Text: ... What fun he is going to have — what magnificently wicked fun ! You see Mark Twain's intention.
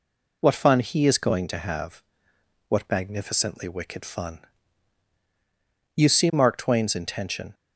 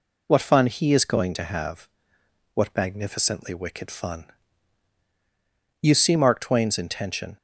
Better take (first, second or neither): neither